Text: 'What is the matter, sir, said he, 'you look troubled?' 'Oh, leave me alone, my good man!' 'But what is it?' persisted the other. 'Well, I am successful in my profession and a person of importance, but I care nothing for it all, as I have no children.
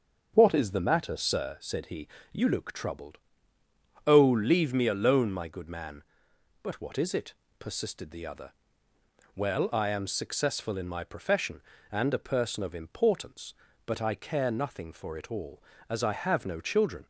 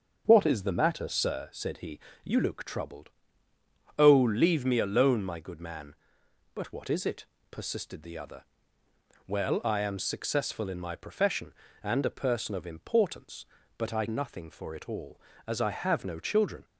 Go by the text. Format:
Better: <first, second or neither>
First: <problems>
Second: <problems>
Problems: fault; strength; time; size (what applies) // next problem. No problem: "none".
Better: first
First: starts louder than the rest; until 1.3 s; 6.5 dB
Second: starts louder than the rest; until 1.2 s; 6.5 dB // skips "care"; at 14.0 s